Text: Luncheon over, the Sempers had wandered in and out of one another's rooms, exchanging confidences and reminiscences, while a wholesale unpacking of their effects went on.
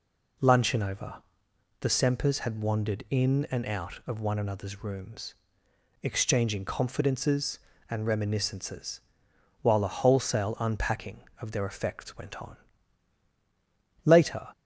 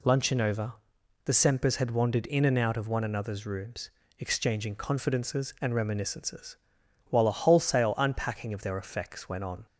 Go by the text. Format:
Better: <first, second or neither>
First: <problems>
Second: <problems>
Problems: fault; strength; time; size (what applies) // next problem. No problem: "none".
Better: second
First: goes on to say "Later"; slight; from 14.0 s on; 0.46 s long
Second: none